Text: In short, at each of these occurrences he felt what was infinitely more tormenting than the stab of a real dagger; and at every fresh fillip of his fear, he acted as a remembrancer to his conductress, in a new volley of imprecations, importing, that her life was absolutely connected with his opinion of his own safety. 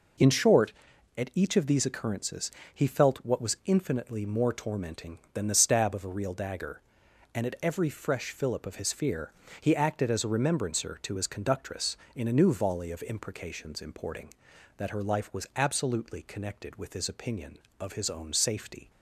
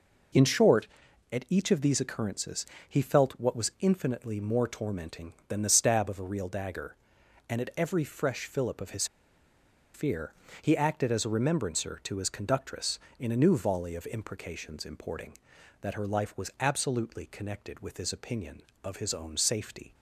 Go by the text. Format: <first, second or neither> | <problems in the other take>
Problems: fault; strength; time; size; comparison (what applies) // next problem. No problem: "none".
first | pauses between "occurrences" and "he"; slight; at 2.6 s; 0.24 s long; slight in the first // pauses between "his" and "fear"; noticeable; at 9.0 s; 0.88 s long